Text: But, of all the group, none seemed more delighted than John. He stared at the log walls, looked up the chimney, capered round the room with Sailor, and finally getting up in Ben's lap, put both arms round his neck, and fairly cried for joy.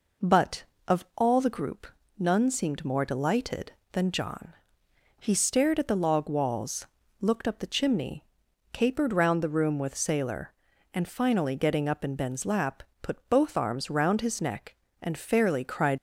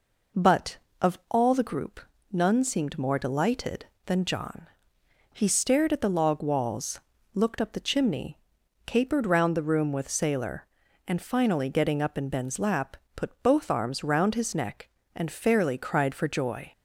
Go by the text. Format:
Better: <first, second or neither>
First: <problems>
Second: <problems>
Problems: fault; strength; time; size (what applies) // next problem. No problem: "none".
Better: second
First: stops before "for joy"; at 15.9 s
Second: none